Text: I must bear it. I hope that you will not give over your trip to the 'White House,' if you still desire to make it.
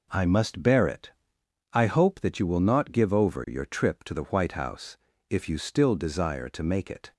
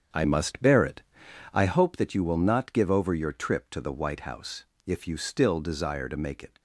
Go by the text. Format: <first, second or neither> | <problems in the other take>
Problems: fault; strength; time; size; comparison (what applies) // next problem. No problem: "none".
first | starts louder than the rest; strong; until 1.8 s; 8 dB